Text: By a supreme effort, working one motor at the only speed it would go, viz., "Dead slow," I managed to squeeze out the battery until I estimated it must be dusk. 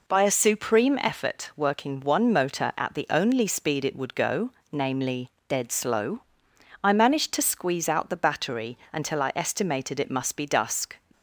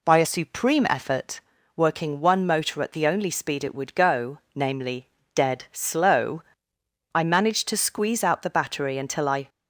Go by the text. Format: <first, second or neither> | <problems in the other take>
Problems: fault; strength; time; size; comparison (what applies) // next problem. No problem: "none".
first | stops before "estimated it must be dusk"; at 9.4 s